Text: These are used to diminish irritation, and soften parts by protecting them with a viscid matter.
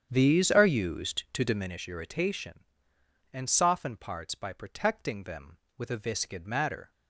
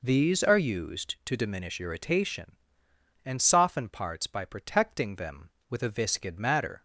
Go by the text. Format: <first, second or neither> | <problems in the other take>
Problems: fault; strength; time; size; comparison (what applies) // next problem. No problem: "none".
second | starts louder than the rest; strong; until 1.8 s; 8.5 dB